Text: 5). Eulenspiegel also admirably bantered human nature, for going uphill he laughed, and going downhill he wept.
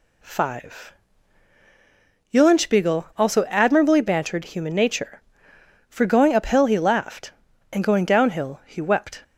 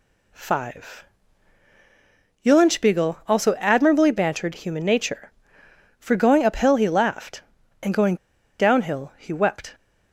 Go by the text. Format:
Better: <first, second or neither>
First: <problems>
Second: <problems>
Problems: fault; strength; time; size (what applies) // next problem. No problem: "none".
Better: first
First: none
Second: pauses between "going" and "downhill"; at 8.1 s; 0.44 s long